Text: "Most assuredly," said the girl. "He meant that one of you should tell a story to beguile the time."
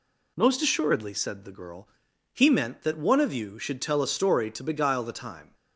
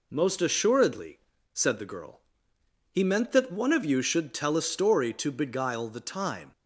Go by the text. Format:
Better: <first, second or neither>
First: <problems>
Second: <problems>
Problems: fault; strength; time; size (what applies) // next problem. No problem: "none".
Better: neither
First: none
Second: none